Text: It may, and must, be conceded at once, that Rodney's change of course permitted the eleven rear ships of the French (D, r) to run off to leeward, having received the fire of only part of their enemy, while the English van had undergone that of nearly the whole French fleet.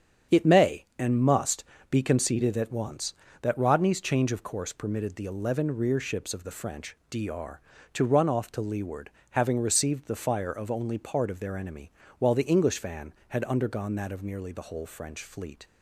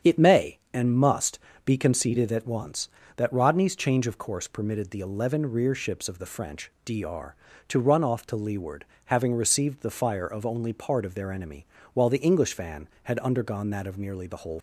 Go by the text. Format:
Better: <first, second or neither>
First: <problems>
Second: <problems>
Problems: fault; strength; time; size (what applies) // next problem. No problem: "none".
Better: first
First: starts louder than the rest; strong; until 1.4 s; 8 dB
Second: starts louder than the rest; strong; until 1.2 s; 8 dB // stops before "French fleet"; at 14.5 s